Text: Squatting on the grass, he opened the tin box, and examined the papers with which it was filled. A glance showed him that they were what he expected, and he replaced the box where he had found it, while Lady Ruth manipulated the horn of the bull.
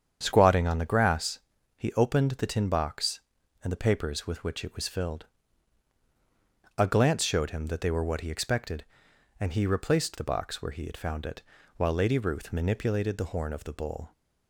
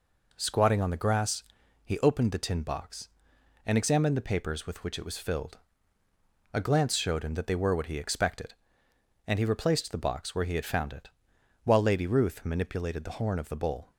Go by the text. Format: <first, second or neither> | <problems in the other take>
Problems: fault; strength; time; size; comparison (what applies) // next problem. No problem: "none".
second | starts louder than the rest; strong; until 1.2 s; 8 dB // skips "examined"; at 3.7 s